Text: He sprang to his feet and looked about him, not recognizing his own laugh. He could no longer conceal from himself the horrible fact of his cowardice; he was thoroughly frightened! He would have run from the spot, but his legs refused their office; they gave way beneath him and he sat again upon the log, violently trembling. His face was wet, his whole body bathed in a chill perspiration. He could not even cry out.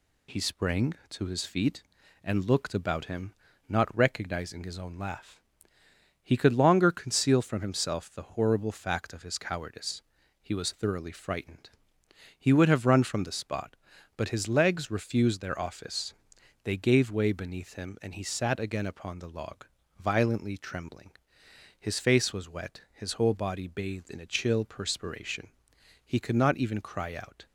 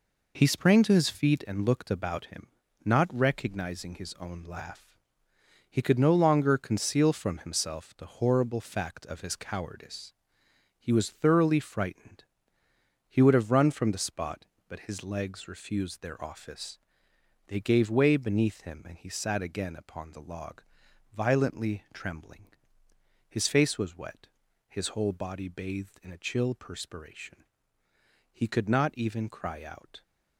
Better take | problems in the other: second | skips "no"; at 6.5 s

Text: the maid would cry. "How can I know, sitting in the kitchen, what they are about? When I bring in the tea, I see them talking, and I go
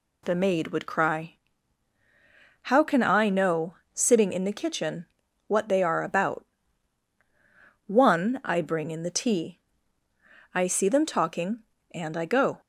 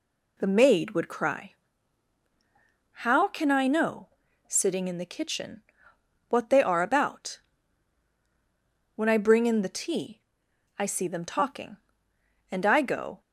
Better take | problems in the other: second | says "One" for "When"; at 7.8 s

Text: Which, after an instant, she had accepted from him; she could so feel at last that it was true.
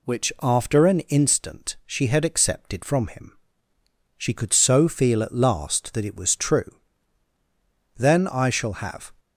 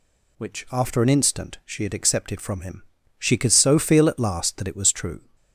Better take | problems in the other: second | goes on to say "Then I shall have"; noticeable; from 7.9 s on; 1.1 s long

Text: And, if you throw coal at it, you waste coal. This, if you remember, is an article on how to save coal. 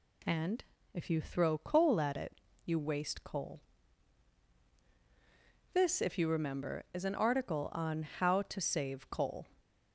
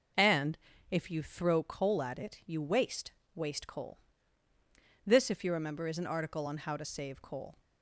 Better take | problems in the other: first | says "waste" twice; at 3.3 s

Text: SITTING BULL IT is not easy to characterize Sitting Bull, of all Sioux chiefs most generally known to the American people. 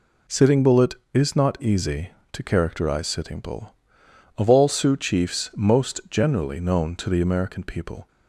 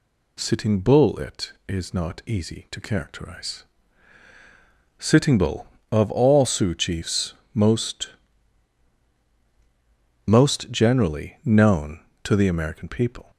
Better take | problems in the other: first | pauses between "characterize" and "Sitting"; strong; at 3.6 s; 1.3 s long // pauses between "chiefs" and "most"; slight; at 7.3 s; 0.20 s long // says "most" twice; at 10.2 s

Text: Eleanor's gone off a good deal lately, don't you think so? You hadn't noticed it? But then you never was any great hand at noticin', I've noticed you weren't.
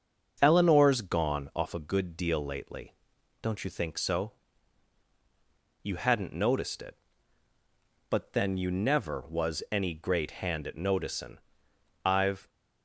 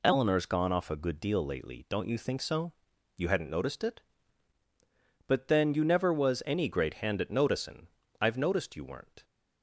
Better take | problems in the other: second | starts louder than the rest; until 1.4 s; 6.5 dB // stops before "noticed you weren't"; at 12.4 s

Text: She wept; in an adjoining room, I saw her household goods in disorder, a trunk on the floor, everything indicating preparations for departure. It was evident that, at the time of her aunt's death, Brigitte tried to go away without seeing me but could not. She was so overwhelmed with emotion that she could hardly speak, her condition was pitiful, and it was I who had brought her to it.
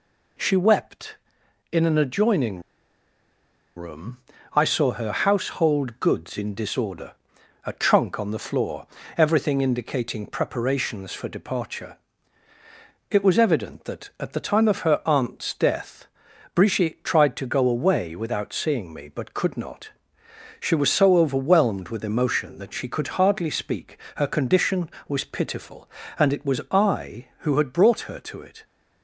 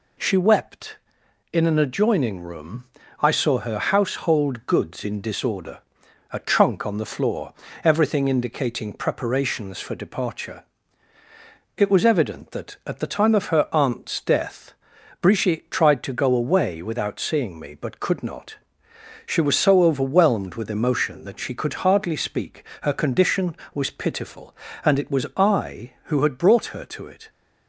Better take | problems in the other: second | pauses between "adjoining" and "room"; at 2.5 s; 1.1 s long

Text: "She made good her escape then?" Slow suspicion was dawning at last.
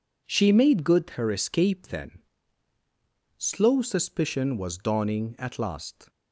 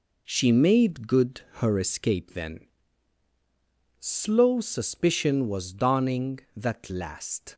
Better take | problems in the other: first | pauses between "good" and "her"; slight; at 1.4 s; 0.20 s long // says "that" for "at"; at 6.5 s

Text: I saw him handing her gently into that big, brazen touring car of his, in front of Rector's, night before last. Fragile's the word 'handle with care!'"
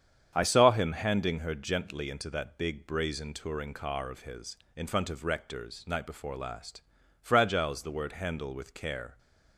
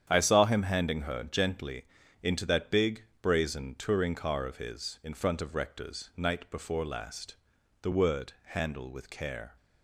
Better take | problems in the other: first | starts louder than the rest; strong; until 1.1 s; 9 dB; strong in the first // pauses between "gently" and "into"; at 1.8 s; 0.38 s long // skips "Fragile's"; at 7.5 s

